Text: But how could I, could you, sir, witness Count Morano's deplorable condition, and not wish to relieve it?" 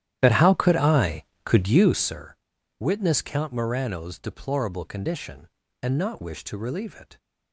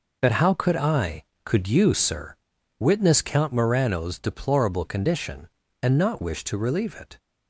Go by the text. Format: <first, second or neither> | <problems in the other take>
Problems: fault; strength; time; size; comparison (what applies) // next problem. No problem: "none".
second | starts louder than the rest; strong; until 2.1 s; 12 dB